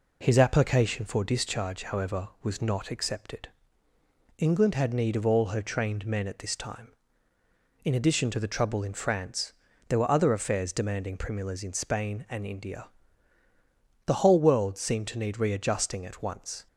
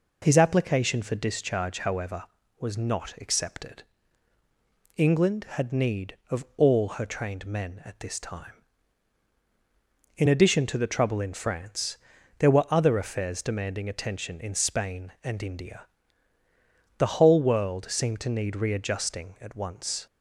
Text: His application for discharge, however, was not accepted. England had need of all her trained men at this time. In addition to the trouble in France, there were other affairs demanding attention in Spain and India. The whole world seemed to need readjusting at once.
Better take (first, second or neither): second